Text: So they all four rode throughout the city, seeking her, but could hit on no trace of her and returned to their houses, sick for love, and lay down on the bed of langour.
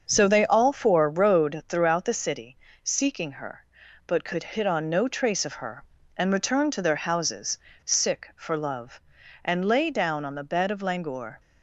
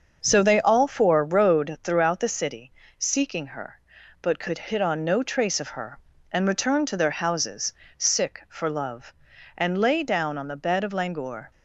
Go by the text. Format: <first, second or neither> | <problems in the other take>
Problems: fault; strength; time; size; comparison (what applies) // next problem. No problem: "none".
neither | starts louder than the rest; the same in both